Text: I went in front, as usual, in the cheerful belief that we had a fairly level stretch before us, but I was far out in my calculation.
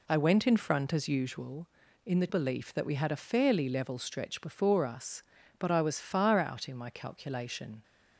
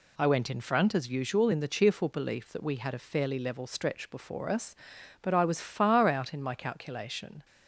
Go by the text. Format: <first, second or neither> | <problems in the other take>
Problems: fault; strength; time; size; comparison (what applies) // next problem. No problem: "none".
second | skips "cheerful"; at 2.2 s